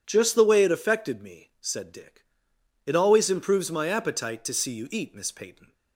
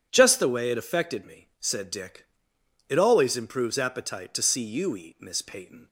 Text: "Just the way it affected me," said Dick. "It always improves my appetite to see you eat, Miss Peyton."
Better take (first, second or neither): first